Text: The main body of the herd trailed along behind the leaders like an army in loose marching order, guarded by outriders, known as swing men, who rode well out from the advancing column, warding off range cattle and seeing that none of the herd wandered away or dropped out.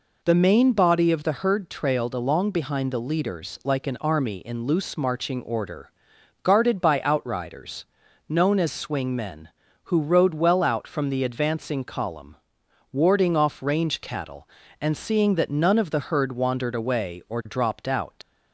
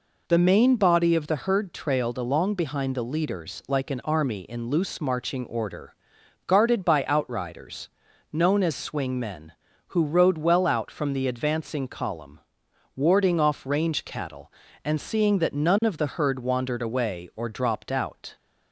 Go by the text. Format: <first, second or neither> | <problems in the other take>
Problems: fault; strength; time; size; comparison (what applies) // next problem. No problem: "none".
second | leaves "out" unfinished; at 18.2 s; 95 ms